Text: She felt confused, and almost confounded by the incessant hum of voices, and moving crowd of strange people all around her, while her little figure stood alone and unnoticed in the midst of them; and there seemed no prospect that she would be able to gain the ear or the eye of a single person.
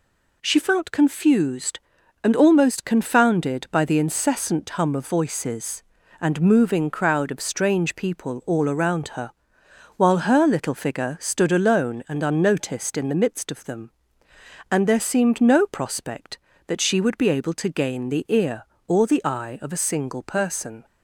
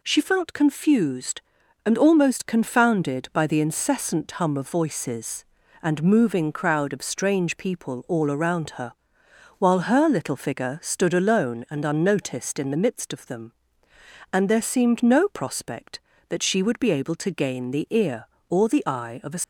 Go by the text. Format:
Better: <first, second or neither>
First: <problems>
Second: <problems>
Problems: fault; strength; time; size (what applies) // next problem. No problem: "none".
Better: first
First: none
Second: stops before "single person"; at 19.4 s